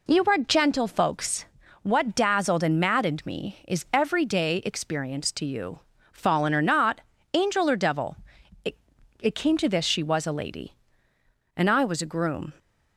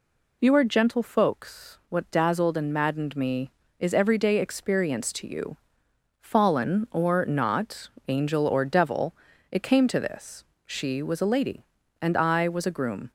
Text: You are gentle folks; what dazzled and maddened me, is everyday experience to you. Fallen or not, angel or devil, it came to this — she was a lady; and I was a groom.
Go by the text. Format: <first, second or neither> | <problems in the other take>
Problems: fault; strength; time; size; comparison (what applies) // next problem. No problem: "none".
second | says "it" twice; at 9.1 s